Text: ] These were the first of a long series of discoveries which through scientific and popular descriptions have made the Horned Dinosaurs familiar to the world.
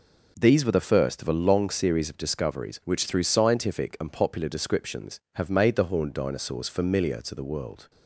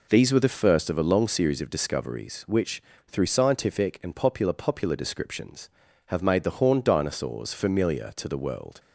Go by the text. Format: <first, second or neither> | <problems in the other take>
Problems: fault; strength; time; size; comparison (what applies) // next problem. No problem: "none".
first | pauses between "which" and "through"; slight; at 2.8 s; 0.26 s long // says "popular" twice; at 4.5 s